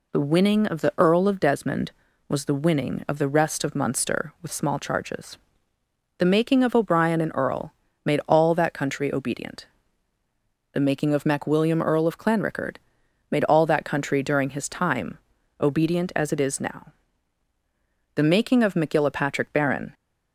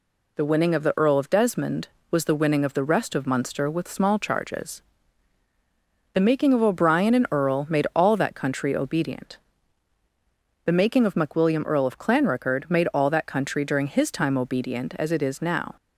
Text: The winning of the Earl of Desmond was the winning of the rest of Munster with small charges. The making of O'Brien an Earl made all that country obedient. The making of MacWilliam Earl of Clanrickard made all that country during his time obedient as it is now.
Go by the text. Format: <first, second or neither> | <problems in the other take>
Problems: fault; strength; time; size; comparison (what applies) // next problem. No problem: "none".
second | pauses between "Earl" and "made"; slight; at 7.7 s; 0.30 s long // pauses between "Clanrickard" and "made"; noticeable; at 12.7 s; 0.52 s long // pauses between "time" and "obedient"; at 15.1 s; 0.42 s long // goes on to say "The making of MacGillapatrick Baron"; strong; from 18.1 s on; 1.7 s long